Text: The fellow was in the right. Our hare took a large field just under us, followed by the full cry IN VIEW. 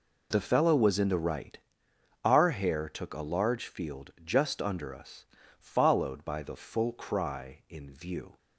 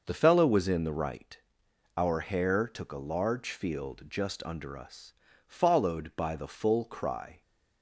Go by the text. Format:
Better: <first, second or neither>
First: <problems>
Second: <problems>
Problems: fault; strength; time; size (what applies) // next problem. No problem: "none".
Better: first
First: none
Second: stops before "IN VIEW"; at 7.4 s